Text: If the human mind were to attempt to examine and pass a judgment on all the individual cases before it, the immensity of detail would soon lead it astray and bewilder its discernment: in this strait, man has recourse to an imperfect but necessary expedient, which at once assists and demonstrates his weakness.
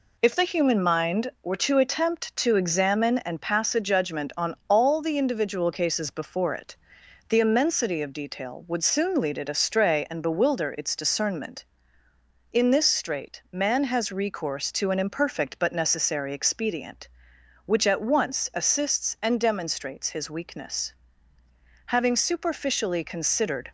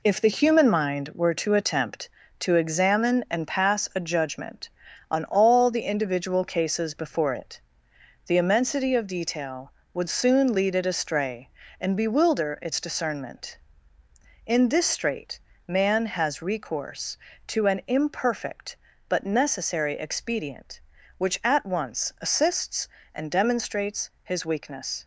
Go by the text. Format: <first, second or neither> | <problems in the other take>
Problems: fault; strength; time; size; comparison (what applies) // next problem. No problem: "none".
second | goes on to say "Having superficially considered"; strong; from 21.8 s on; 1.8 s long